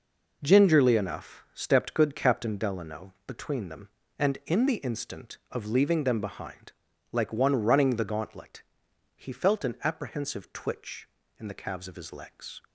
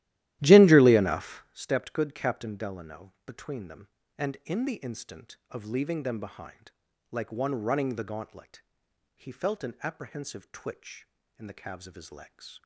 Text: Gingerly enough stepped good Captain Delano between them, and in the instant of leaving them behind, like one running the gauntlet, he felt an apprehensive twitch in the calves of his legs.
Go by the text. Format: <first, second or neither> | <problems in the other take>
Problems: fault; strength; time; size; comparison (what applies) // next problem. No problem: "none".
first | starts louder than the rest; strong; until 1.5 s; 14.5 dB